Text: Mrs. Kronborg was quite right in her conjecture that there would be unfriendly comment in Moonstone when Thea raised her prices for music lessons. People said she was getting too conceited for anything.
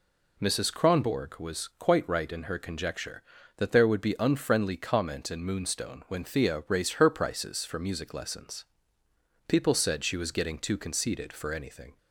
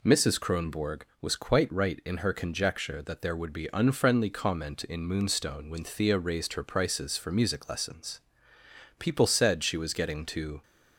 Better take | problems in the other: first | stops before "conceited for anything"; at 10.6 s

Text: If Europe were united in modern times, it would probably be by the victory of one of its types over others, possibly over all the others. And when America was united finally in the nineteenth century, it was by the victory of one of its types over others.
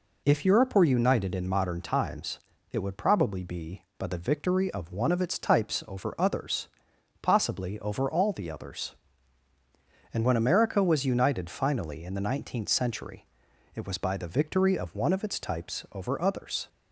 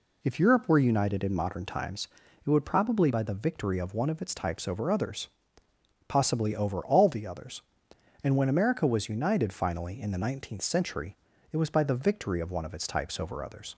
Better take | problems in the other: first | skips "be"; at 3.0 s

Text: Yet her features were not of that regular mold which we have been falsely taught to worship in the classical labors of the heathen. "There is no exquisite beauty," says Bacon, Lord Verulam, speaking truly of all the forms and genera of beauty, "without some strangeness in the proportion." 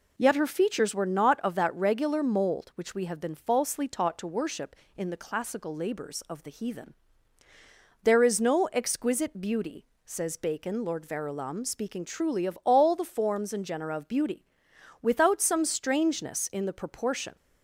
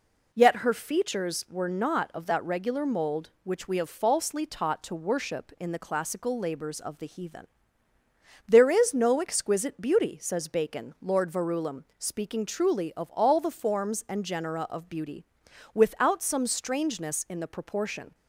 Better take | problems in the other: first | skips "been"; at 3.9 s

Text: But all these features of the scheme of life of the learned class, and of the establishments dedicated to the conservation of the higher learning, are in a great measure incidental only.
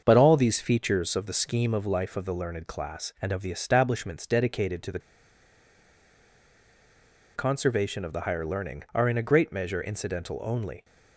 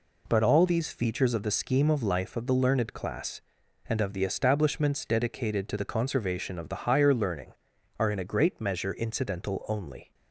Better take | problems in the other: second | starts louder than the rest; until 1.0 s; 6.5 dB // pauses between "the" and "conservation"; strong; at 4.9 s; 2.3 s long

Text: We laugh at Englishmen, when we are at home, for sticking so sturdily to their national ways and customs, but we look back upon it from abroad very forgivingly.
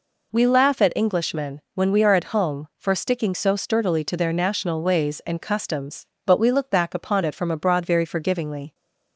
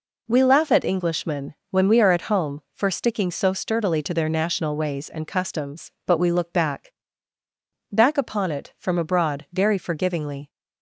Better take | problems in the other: first | says "back" twice; at 7.9 s

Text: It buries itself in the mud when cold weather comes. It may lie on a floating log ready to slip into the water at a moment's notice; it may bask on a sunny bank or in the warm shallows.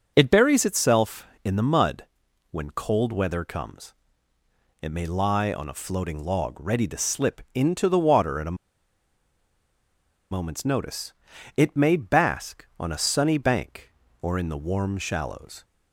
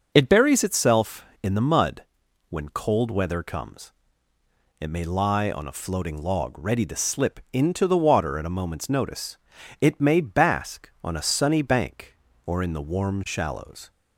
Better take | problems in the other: second | starts louder than the rest; until 1.1 s; 6.5 dB; also in the second // pauses between "mud" and "when"; noticeable; at 2.0 s; 0.48 s long; noticeable in the second // pauses between "a" and "moment's"; strong; at 8.5 s; 1.7 s long

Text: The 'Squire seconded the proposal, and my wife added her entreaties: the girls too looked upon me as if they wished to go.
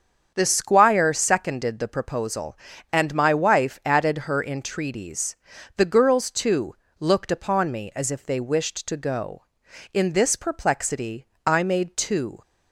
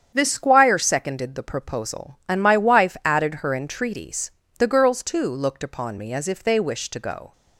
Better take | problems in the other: second | starts louder than the rest; strong; until 1.3 s; 7.5 dB; strong in the second // pauses between "too" and "looked"; slight; at 6.7 s; 0.26 s long // goes on to say "In this perplexity I made two"; strong; from 9.9 s on; 2.4 s long

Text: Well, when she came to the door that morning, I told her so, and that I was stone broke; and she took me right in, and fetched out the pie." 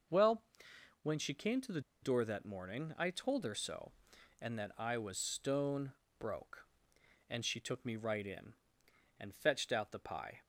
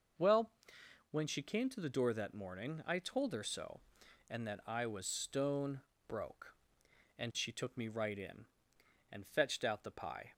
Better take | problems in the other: second | pauses between "the" and "door"; slight; at 1.7 s; 0.22 s long // pauses between "stone" and "broke"; slight; at 5.9 s; 0.28 s long; slight in the second

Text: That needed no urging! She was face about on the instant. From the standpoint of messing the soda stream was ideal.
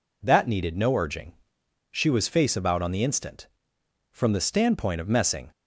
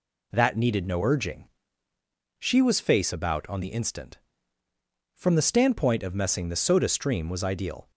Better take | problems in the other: second | stops before "the soda stream was ideal"; at 5.5 s

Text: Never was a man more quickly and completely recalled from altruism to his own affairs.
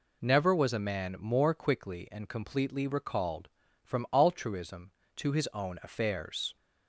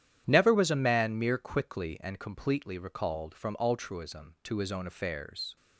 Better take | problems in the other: first | starts louder than the rest; strong; until 1.3 s; 10 dB // says "mere" for "more"; at 1.1 s

